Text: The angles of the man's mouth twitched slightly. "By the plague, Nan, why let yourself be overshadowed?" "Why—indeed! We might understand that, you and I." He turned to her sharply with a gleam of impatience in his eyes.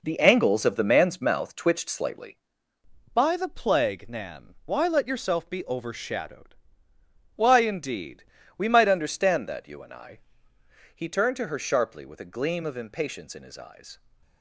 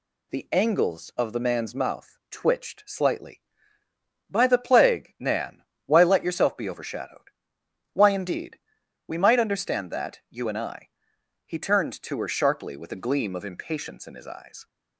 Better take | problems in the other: second | gets quieter; strong; throughout; 7.5 dB

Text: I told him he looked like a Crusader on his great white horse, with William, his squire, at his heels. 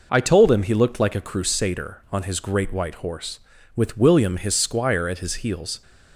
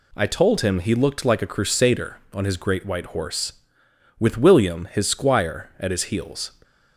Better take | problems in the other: neither | none

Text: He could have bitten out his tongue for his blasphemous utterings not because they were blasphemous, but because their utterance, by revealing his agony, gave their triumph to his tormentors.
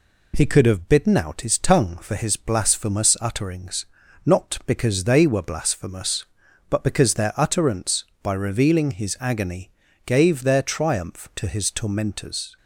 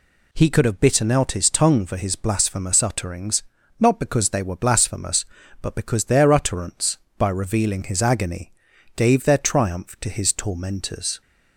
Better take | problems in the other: neither | pauses between "utterings" and "not"; the same in both

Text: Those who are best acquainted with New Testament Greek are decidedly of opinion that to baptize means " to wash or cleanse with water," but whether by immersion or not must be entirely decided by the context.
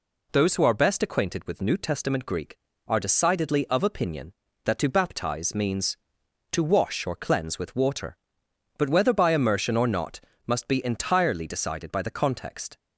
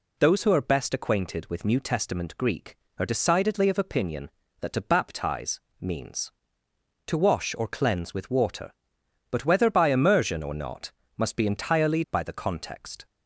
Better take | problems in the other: first | pauses between "baptize" and "means"; slight; at 5.5 s; 0.22 s long // pauses between "not" and "must"; slight; at 10.9 s; 0.26 s long; slight in the first // skips "decided"; at 12.0 s

